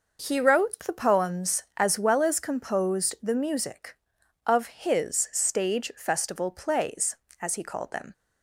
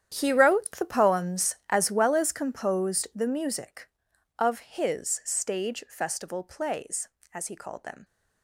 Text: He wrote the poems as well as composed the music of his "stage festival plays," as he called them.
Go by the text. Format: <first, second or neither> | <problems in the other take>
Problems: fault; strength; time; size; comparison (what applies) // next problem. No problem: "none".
first | gets quieter; strong; throughout; 15 dB